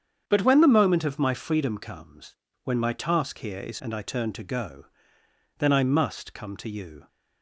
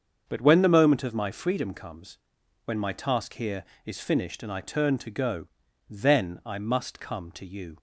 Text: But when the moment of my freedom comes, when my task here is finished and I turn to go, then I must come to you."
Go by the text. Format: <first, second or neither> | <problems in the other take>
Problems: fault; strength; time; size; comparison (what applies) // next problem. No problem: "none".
second | starts louder than the rest; strong; until 1.2 s; 8 dB; also in the second // skips "finished"; at 3.8 s